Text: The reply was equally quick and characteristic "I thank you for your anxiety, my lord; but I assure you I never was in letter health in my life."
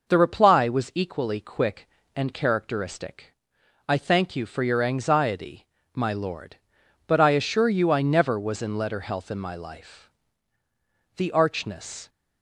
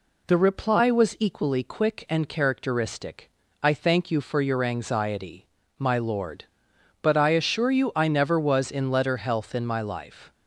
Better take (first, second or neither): second